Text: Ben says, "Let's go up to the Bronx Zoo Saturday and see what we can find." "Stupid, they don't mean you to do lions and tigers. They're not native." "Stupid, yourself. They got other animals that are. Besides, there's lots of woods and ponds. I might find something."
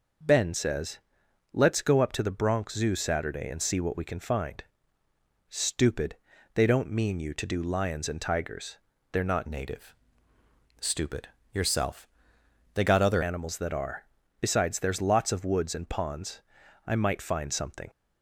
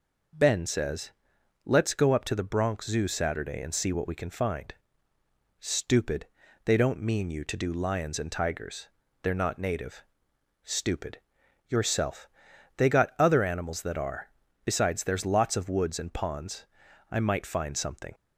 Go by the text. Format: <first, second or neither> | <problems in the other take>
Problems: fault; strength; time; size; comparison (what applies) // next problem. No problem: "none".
second | changes voice from "native" to "other"; from 9.4 to 13.2 s; 3.8 s long